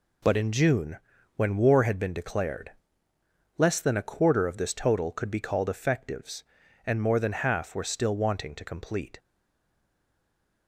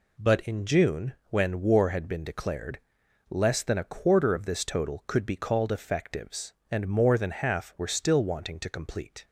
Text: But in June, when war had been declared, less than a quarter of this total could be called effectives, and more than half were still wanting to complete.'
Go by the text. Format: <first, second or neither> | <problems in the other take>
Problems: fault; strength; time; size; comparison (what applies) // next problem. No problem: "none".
second | stays silent after the last word; noticeable; from 9.1 s on; 1.5 s long